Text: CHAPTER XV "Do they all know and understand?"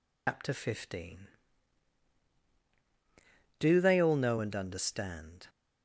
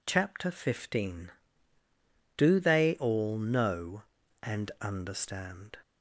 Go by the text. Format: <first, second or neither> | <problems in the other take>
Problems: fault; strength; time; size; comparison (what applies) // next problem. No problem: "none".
second | loses the start of "CHAPTER"; at 0.2 s; 150 ms